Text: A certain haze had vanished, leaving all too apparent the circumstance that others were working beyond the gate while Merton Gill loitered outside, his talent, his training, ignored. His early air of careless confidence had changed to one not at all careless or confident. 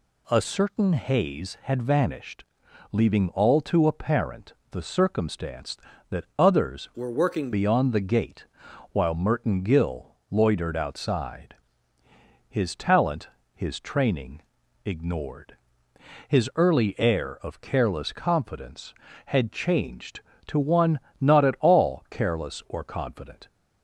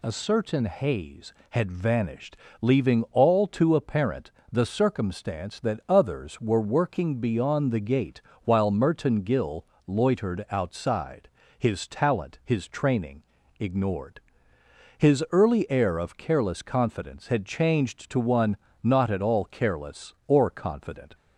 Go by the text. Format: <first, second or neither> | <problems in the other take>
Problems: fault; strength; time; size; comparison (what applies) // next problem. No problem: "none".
second | pauses between "apparent" and "the"; slight; at 4.5 s; 0.18 s long; slight in the second // changes voice from "were" to "working"; from 6.9 to 7.5 s; 0.6 s long // pauses between "gate" and "while"; noticeable; at 8.4 s; 0.46 s long; slight in the second // pauses between "Gill" and "loitered"; slight; at 10.1 s; 0.16 s long; slight in the second // pauses between "one" and "not"; slight; at 20.9 s; 0.20 s long; slight in the second